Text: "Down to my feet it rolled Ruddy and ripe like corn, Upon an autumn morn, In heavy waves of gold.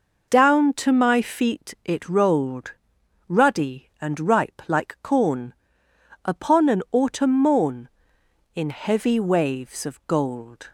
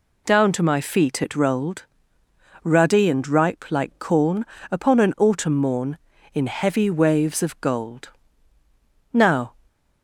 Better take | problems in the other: first | pauses between "rolled" and "Ruddy"; noticeable; at 1.8 s; 0.78 s long; noticeable in the first // goes on to say "Now"; slight; from 9.1 s on; 0.42 s long

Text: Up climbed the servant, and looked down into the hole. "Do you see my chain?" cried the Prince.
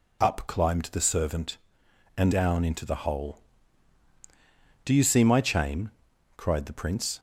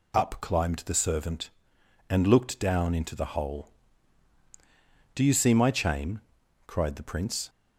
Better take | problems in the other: second | skips "looked"; at 2.3 s

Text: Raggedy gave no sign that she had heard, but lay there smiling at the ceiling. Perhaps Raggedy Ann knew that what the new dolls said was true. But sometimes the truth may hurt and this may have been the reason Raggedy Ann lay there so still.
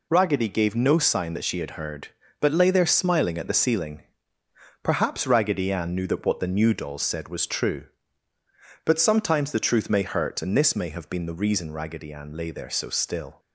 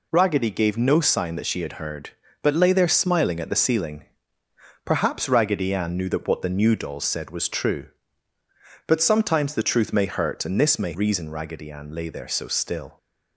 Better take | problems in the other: first | skips "have been the"; at 10.9 s

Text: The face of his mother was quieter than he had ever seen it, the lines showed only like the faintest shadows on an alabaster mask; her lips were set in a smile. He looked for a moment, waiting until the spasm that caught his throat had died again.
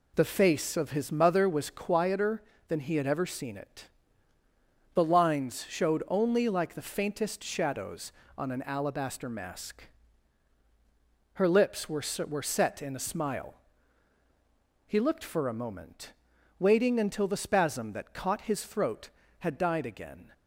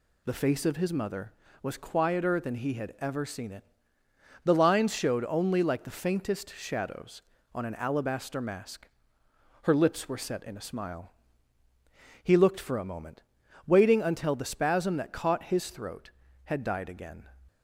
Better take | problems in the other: second | says "were" twice; at 12.2 s

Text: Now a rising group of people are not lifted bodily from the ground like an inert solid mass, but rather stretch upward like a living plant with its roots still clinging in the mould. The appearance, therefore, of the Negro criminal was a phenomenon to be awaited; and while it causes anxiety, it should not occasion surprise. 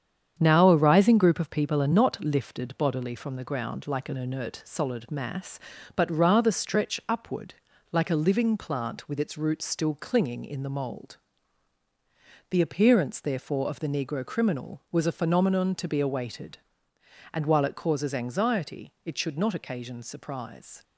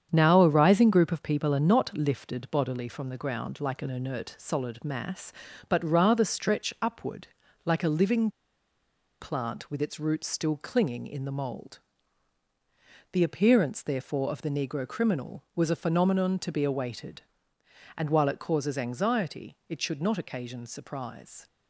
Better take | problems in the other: first | starts louder than the rest; strong; until 1.1 s; 8 dB; strong in the first // pauses between "upward" and "like"; slight; at 7.2 s; 0.36 s long; slight in the first // pauses between "living" and "plant"; noticeable; at 8.2 s; 0.92 s long

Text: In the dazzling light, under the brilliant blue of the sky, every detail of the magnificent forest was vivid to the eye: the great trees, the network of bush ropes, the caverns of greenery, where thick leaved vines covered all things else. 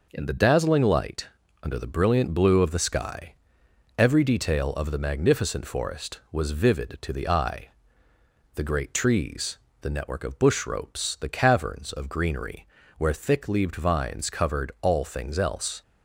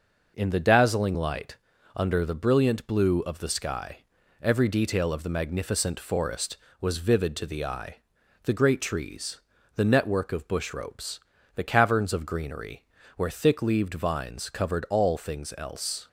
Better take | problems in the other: neither | none

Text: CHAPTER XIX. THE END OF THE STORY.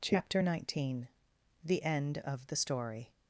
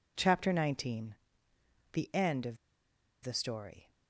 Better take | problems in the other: first | pauses between "OF" and "THE"; noticeable; at 2.5 s; 0.67 s long

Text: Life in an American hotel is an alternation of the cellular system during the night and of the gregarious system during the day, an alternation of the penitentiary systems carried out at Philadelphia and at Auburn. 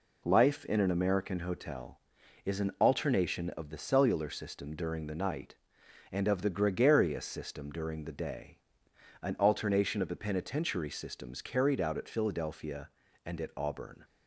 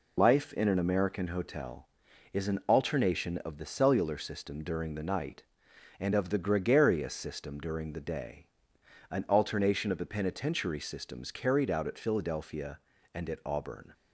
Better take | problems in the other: first | loses the start of "Life"; at 0.1 s; 50 ms

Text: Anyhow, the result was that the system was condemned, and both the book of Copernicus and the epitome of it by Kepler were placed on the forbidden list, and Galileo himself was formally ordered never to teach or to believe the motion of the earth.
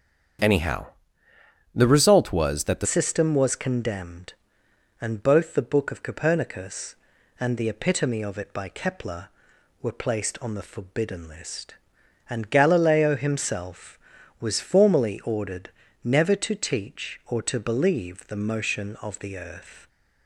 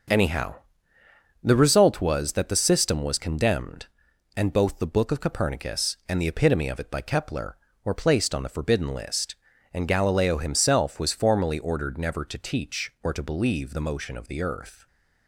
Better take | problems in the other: second | starts louder than the rest; strong; until 2.2 s; 7.5 dB; noticeable in the second // changes voice at "system"; from 2.8 s on; 17.0 s long // pauses between "ordered" and "never"; slight; at 15.7 s; 0.34 s long

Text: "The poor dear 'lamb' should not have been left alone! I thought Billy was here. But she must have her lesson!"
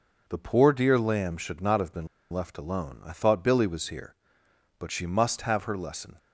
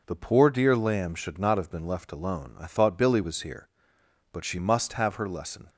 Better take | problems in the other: second | pauses between "been" and "left"; slight; at 2.0 s; 0.24 s long

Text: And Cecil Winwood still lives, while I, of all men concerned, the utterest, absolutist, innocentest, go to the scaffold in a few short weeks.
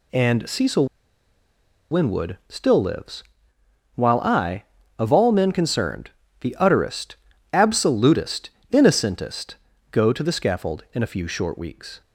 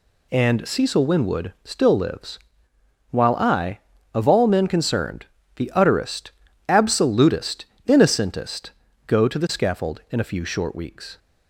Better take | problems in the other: second | pauses between "Cecil" and "Winwood"; at 0.8 s; 1.0 s long

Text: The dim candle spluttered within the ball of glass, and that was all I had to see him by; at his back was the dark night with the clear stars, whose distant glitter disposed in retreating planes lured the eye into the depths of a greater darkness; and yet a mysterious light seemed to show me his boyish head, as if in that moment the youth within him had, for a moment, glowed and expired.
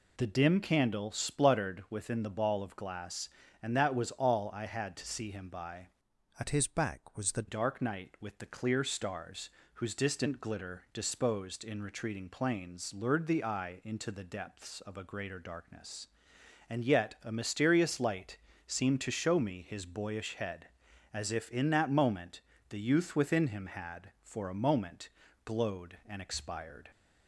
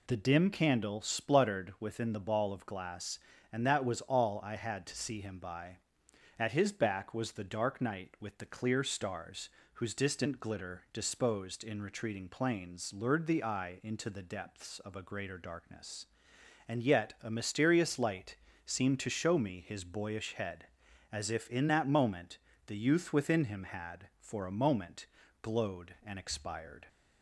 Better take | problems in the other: second | changes voice from "at" to "the"; from 6.3 to 7.4 s; 1.1 s long // pauses between "light" and "seemed"; slight; at 18.3 s; 0.28 s long; slight in the second // pauses between "moment" and "the"; slight; at 22.4 s; 0.30 s long; slight in the second

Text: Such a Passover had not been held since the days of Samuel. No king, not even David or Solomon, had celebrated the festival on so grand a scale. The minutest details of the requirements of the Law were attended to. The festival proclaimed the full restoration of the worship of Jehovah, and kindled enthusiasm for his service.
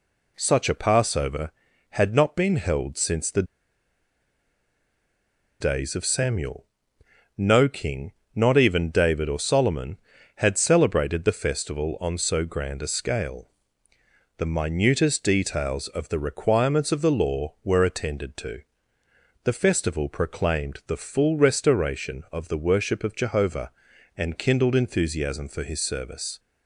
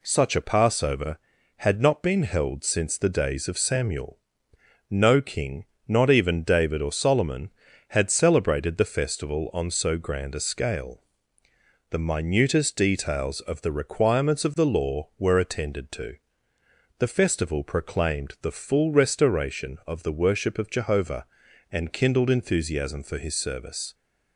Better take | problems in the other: second | pauses between "the" and "days"; strong; at 3.4 s; 2.1 s long

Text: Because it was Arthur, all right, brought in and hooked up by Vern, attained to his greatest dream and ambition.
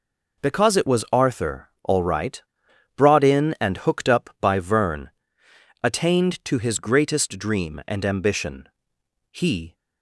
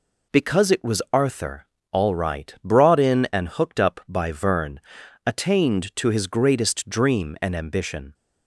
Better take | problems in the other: second | goes on to say "He"; slight; from 9.2 s on; 0.46 s long

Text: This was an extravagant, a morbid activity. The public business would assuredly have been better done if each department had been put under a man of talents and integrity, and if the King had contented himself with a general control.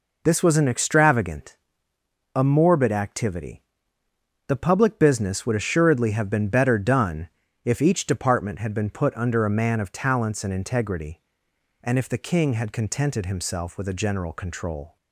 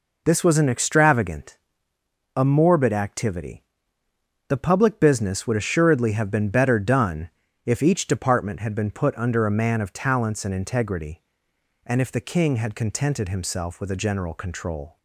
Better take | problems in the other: neither | pauses between "done" and "if"; slight; the same in both

